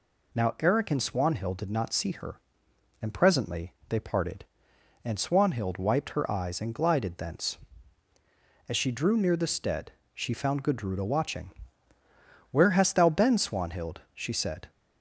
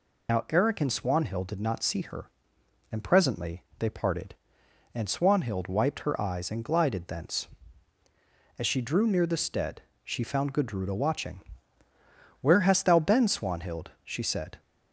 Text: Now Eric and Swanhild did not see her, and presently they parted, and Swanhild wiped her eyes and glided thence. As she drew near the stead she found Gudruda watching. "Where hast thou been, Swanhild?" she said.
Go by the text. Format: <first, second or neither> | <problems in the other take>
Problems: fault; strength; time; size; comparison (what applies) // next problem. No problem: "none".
first | loses the start of "Now"; at 0.2 s; 60 ms // pauses between "presently" and "they"; slight; at 3.6 s; 0.16 s long; slight in the first // pauses between "stead" and "she"; slight; at 9.8 s; 0.22 s long; slight in the first